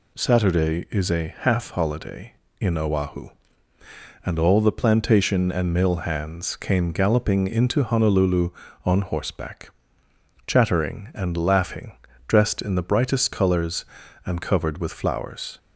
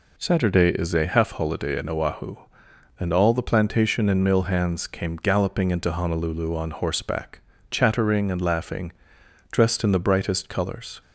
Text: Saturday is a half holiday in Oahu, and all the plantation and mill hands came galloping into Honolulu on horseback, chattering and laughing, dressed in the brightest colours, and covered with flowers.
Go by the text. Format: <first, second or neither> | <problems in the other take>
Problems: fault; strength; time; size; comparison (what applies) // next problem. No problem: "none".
first | stops before "and covered with flowers"; at 11.0 s